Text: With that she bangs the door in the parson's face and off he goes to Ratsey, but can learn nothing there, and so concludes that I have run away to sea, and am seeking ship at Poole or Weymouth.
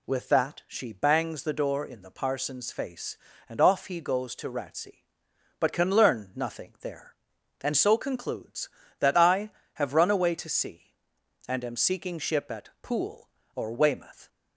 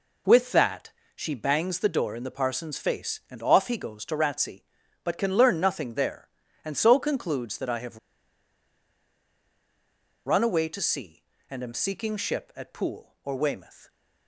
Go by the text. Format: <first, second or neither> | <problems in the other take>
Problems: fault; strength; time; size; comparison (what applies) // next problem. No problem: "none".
first | pauses between "that" and "she"; slight; at 0.8 s; 0.24 s long // pauses between "have" and "run"; strong; at 7.9 s; 2.2 s long